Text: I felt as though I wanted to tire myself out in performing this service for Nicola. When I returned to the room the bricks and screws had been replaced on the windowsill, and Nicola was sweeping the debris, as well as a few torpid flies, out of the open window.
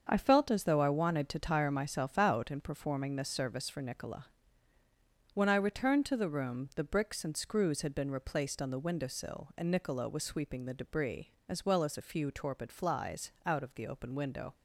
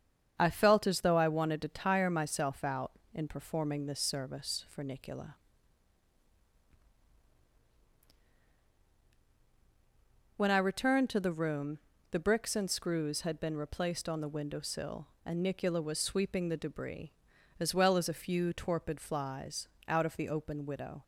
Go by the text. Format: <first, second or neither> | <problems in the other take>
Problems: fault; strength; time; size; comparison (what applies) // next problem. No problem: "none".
first | starts louder than the rest; strong; until 1.3 s; 7.5 dB; also in the first // pauses between "room" and "the"; slight; at 11.7 s; 0.32 s long // says "widow" for "window"; at 20.6 s